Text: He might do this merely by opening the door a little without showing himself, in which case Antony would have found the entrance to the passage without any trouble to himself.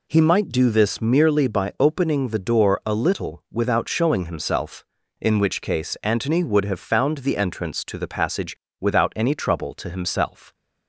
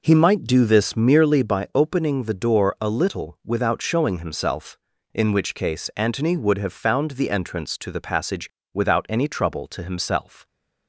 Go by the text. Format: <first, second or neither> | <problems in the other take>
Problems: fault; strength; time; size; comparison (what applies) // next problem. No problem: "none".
first | starts louder than the rest; noticeable; until 1.6 s; 4.5 dB // pauses between "passage" and "without"; slight; at 8.4 s; 0.24 s long; slight in the first